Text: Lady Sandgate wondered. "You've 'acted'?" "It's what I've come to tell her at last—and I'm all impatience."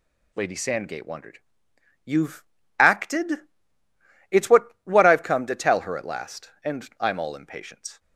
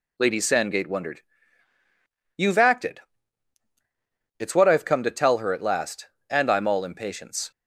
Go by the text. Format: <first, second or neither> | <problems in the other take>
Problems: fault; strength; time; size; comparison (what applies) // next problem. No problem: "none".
second | pauses between "You've" and "acted"; slight; at 2.4 s; 0.36 s long // says "what" twice; at 4.8 s